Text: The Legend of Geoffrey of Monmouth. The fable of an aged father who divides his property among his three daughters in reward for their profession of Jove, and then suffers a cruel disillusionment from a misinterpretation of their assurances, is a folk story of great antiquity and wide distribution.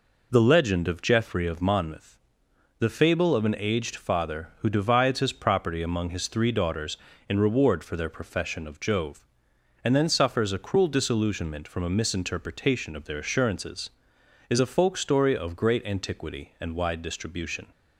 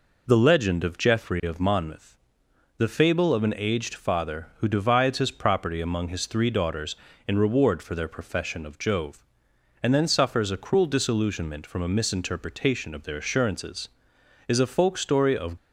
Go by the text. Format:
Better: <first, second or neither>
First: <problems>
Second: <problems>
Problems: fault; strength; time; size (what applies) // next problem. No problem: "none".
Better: first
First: none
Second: stops before "great antiquity and wide distribution"; at 15.5 s